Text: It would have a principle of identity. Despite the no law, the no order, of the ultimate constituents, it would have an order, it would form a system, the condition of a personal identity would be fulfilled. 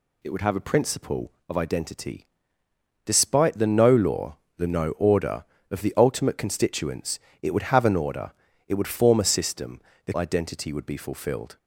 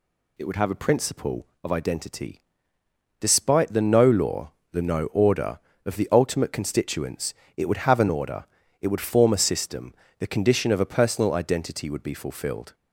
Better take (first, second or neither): second